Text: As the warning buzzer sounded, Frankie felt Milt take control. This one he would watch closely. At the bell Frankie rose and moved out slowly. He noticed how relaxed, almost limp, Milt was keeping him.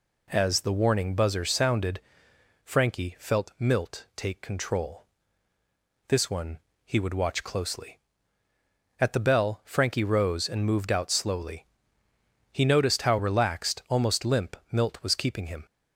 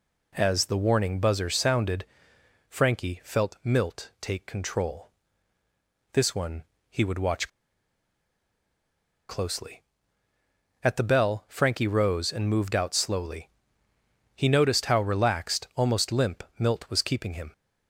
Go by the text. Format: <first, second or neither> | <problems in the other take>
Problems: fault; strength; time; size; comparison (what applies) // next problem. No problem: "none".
first | pauses between "one" and "he"; slight; at 6.6 s; 0.26 s long; slight in the first // pauses between "watch" and "closely"; strong; at 7.4 s; 1.8 s long